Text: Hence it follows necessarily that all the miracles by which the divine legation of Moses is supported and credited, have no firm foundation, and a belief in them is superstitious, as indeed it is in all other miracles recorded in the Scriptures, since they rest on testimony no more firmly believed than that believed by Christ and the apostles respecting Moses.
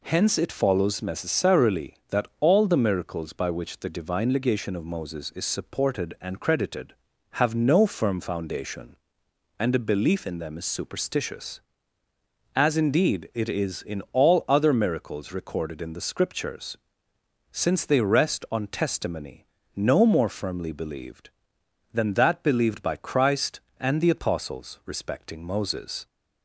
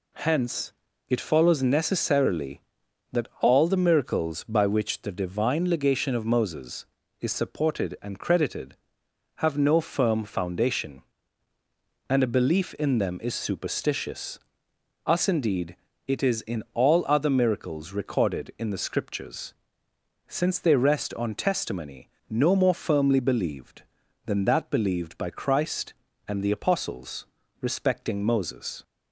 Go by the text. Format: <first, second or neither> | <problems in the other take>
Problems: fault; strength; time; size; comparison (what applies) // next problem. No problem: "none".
first | pauses between "Hence" and "it"; slight; at 0.7 s; 0.36 s long // says "us" for "as"; at 15.0 s // pauses between "indeed" and "it"; slight; at 15.7 s; 0.30 s long // pauses between "testimony" and "no"; slight; at 22.0 s; 0.20 s long; slight in the first // pauses between "apostles" and "respecting"; slight; at 27.2 s; 0.36 s long